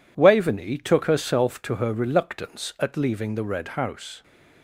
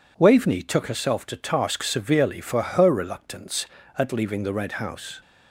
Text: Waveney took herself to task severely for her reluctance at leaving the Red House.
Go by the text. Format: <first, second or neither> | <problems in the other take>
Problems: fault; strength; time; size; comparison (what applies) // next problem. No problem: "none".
second | skips "task severely for"; at 1.7 s